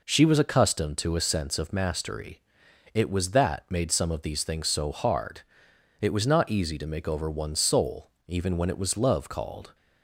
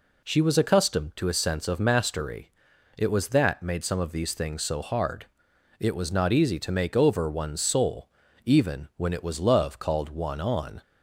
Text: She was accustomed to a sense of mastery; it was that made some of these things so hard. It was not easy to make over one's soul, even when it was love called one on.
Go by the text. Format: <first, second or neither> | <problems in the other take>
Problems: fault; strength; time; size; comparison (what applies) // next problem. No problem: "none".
second | stops before "one on"; at 9.7 s